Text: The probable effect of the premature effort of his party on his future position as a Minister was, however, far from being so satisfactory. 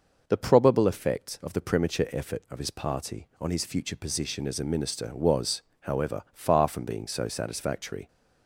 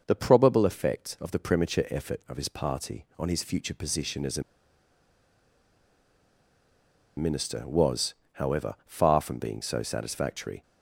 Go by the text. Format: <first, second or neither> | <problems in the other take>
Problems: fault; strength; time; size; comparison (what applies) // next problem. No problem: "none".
first | pauses between "a" and "Minister"; strong; at 4.4 s; 2.7 s long